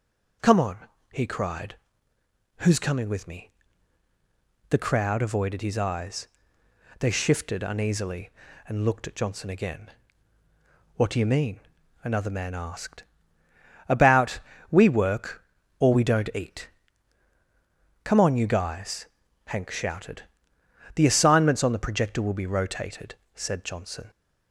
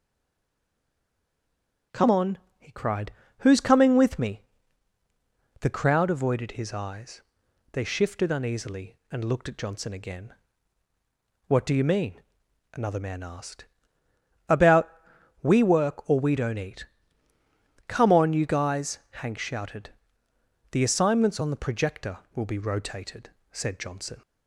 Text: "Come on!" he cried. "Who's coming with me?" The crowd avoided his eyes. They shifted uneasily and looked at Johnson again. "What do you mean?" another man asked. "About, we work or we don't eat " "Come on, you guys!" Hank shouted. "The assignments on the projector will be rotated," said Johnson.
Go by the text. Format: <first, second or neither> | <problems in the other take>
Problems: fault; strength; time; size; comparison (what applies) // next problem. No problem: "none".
first | stays silent before the first word; noticeable; until 1.9 s; 1.9 s long